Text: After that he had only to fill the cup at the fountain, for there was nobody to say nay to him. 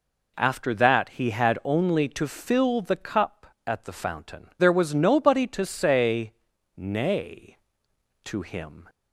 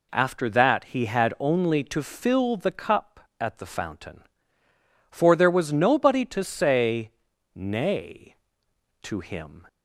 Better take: second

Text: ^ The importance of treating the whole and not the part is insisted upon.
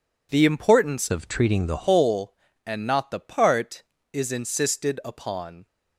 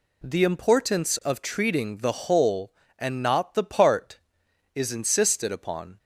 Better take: second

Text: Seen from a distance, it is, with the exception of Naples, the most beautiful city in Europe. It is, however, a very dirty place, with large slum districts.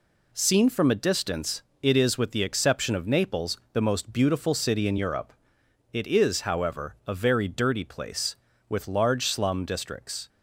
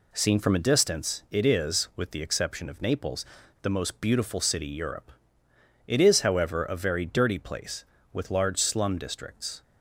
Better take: first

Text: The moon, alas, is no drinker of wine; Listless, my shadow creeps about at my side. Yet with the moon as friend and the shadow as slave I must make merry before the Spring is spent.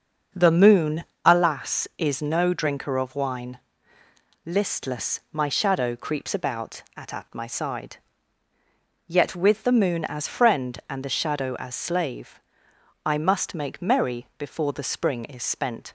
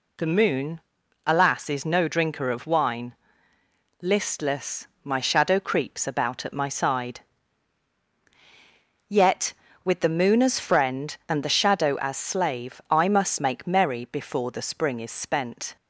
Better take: second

